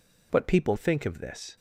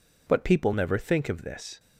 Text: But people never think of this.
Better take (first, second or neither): second